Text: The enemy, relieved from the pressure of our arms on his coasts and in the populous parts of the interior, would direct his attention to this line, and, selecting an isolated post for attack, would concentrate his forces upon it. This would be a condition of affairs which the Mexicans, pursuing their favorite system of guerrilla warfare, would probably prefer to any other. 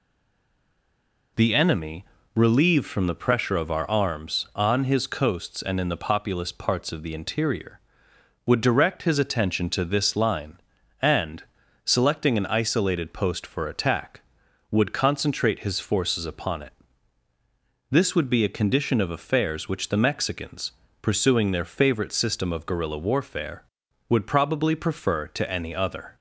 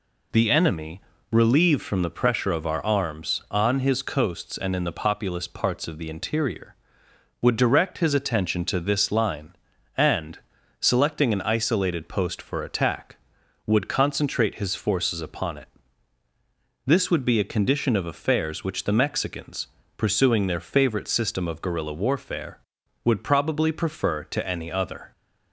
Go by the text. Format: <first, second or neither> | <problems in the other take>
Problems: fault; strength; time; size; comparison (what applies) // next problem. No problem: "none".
second | stays silent before the first word; noticeable; until 1.3 s; 1.3 s long